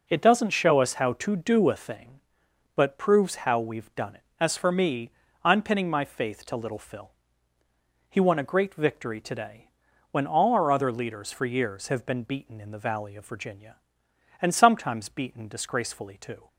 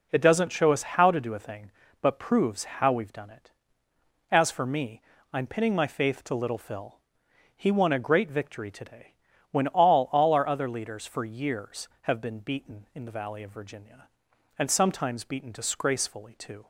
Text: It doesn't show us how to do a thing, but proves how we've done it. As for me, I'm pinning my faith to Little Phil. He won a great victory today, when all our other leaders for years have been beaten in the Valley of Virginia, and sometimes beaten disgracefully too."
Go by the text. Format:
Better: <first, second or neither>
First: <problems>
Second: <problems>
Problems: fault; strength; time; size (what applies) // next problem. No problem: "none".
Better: first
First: none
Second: says "all" twice; at 10.1 s